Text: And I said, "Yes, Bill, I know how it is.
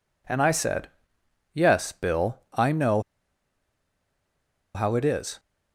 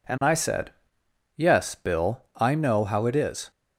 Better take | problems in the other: second | pauses between "know" and "how"; strong; at 3.0 s; 1.7 s long

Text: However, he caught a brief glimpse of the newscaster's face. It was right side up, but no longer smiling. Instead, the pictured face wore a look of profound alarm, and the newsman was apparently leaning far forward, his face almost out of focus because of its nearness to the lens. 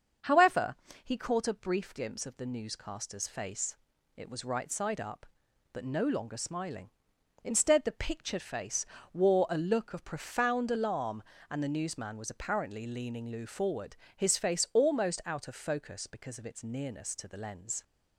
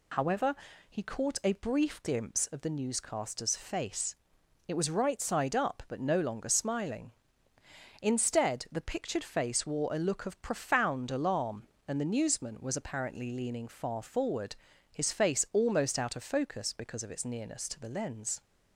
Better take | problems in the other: second | starts louder than the rest; until 1.5 s; 7 dB // pauses between "face" and "wore"; slight; at 8.8 s; 0.26 s long // says "lou" for "far"; at 13.2 s

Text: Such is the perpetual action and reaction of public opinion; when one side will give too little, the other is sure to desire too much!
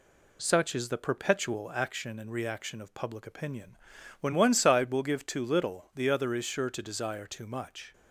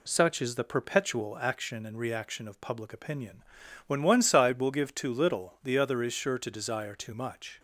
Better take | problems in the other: neither | none

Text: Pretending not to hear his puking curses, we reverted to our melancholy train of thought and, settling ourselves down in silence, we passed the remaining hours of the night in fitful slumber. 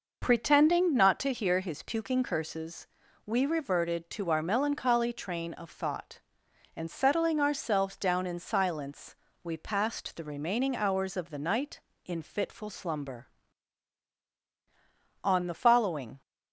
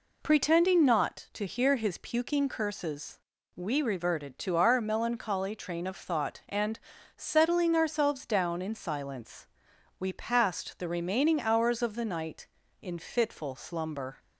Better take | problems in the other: second | goes on to say "On the following"; noticeable; from 15.2 s on; 0.96 s long

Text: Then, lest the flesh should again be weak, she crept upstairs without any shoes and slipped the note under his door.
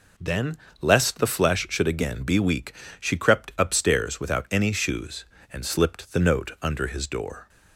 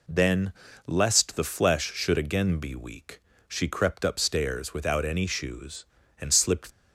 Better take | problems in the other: first | stops before "the note under his door"; at 6.7 s

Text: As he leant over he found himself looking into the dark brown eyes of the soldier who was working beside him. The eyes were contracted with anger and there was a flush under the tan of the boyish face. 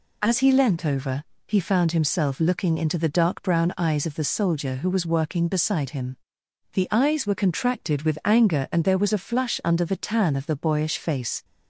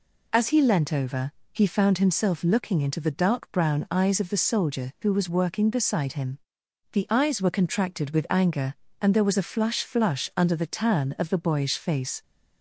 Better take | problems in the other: first | pauses between "over" and "he"; slight; at 1.3 s; 0.20 s long; slight in the first // says "flush" twice; at 9.8 s

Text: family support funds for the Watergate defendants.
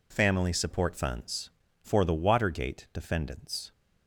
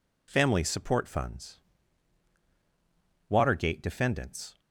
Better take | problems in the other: first | skips "for the"; at 2.4 s

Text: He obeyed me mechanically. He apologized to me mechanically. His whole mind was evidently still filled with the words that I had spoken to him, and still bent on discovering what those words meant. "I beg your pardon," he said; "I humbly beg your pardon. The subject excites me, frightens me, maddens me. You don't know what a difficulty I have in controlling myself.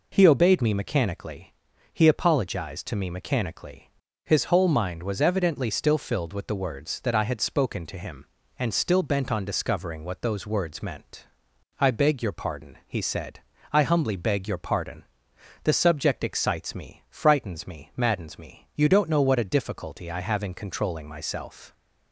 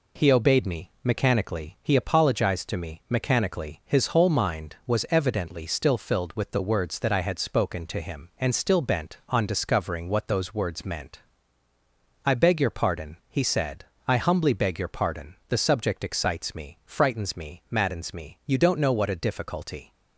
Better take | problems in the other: first | stops before "I have in controlling myself"; at 19.9 s

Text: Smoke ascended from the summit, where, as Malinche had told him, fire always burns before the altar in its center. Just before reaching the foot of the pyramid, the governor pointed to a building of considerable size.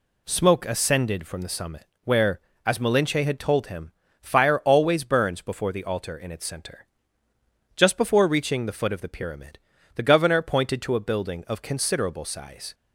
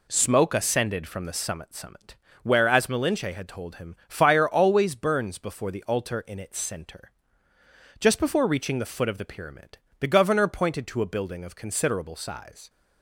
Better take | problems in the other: first | says "summit" twice; at 1.7 s

